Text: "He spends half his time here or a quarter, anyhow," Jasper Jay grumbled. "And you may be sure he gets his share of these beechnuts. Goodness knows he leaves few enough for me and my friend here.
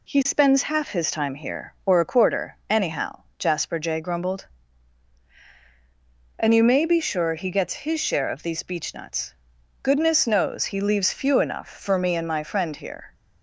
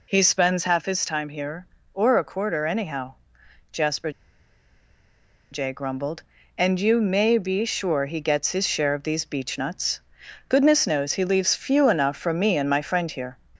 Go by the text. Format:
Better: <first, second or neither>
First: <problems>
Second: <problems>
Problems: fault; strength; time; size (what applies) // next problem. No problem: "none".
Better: first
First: none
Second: pauses between "Jasper" and "Jay"; strong; at 4.0 s; 1.4 s long